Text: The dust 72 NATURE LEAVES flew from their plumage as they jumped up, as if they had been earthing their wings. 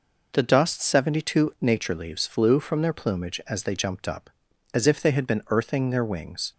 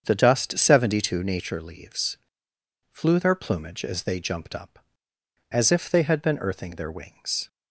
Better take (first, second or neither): first